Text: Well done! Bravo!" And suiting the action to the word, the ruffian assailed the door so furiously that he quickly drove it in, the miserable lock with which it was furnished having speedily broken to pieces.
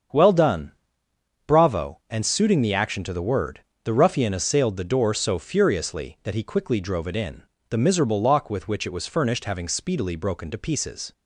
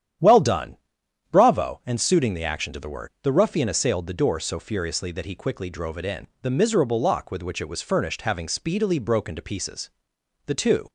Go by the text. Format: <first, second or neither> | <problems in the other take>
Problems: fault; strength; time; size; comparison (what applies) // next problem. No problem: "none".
first | starts louder than the rest; strong; until 1.7 s; 10 dB; strong in the first // goes on to say "The two"; slight; from 10.4 s on; 0.44 s long